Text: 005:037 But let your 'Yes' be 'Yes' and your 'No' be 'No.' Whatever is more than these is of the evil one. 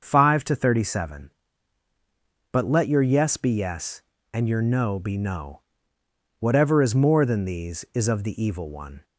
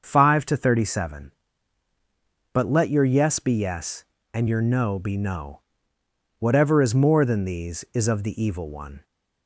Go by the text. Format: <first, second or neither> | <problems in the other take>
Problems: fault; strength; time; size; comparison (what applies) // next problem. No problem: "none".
neither | starts louder than the rest; the same in both